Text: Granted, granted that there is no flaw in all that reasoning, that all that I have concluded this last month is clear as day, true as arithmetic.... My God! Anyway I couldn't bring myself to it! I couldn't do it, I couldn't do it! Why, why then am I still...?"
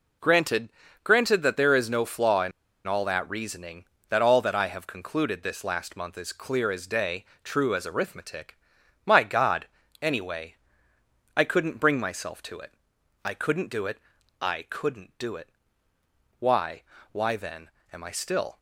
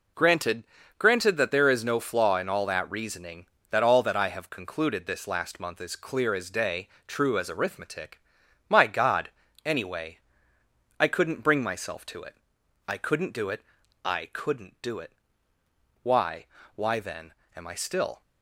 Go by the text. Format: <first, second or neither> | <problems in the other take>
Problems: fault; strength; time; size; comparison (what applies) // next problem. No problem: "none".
second | pauses between "in" and "all"; slight; at 2.5 s; 0.35 s long // pauses between "Anyway" and "I"; noticeable; at 10.5 s; 0.80 s long; noticeable in the second // pauses between "then" and "am"; slight; at 17.7 s; 0.20 s long; slight in the second